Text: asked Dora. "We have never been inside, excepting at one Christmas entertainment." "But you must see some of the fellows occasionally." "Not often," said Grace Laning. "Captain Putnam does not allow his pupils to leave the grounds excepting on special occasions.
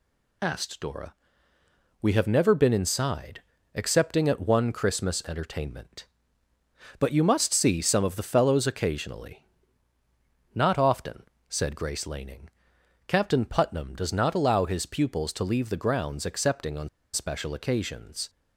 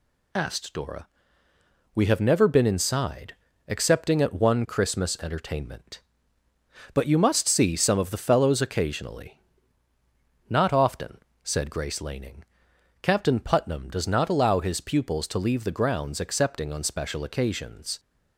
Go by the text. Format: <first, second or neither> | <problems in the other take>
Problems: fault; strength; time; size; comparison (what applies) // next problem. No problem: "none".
second | pauses between "on" and "special"; slight; at 16.8 s; 0.24 s long